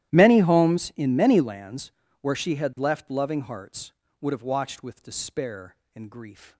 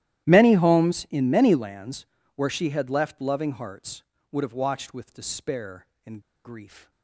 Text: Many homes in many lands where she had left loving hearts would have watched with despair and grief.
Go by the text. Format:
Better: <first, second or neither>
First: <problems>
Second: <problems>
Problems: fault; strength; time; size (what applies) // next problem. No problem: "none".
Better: first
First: starts louder than the rest; strong; until 1.1 s; 13.5 dB // pauses between "lands" and "where"; slight; at 1.8 s; 0.32 s long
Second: starts louder than the rest; strong; until 1.2 s; 13.5 dB // pauses between "lands" and "where"; slight; at 2.0 s; 0.32 s long // pauses between "and" and "grief"; slight; at 6.2 s; 0.24 s long